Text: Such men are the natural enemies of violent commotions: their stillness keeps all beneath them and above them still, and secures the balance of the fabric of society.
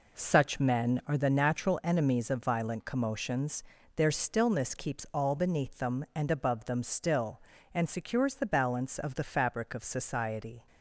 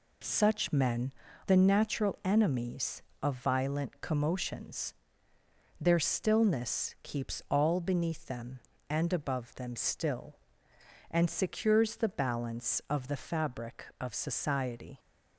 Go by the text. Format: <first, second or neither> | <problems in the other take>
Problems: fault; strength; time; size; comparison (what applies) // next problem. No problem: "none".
first | skips "are"; at 1.2 s